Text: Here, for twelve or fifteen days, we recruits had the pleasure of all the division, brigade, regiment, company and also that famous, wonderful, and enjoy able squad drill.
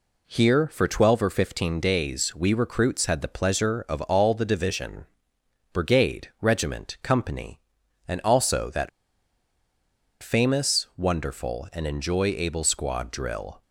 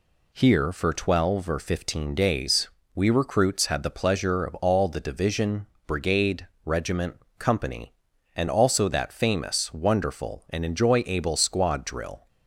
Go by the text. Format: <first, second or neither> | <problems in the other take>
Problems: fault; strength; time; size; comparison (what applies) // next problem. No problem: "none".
second | pauses between "that" and "famous"; strong; at 8.8 s; 1.3 s long